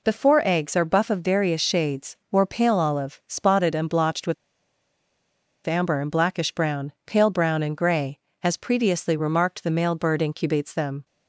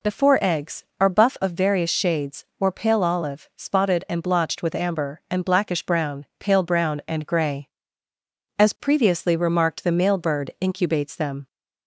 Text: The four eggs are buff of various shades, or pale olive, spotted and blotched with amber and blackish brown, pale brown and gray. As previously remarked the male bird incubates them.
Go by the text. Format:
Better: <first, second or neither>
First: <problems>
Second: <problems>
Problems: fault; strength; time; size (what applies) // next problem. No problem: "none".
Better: second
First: pauses between "with" and "amber"; strong; at 4.3 s; 1.3 s long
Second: none